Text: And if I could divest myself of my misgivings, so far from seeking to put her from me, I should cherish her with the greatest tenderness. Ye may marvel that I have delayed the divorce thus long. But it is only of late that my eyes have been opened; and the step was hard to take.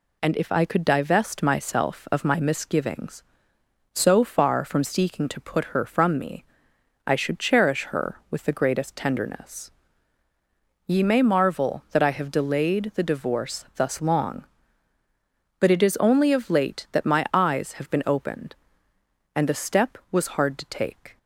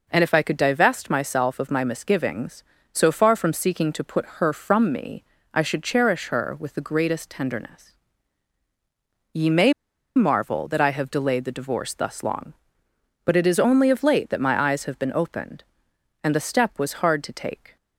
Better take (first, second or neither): first